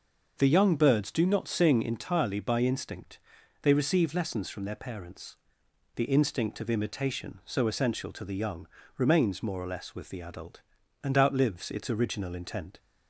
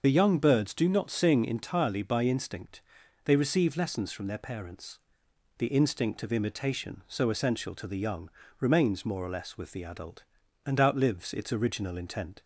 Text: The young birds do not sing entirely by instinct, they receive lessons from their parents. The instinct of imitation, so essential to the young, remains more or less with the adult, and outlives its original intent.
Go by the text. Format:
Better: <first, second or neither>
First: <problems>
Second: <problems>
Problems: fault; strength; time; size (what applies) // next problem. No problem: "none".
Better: first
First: starts louder than the rest; until 1.3 s; 6 dB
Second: loses the start of "The"; at 0.0 s; 30 ms // starts louder than the rest; noticeable; until 1.0 s; 6 dB